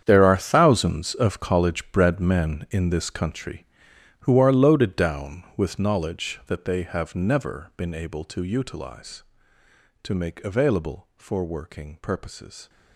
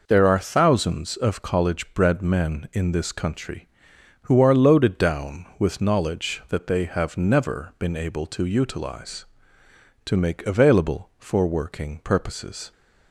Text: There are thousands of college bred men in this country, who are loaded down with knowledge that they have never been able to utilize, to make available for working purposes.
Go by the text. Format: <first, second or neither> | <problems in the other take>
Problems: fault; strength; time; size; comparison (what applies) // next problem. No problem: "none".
second | gets quieter; strong; throughout; 15 dB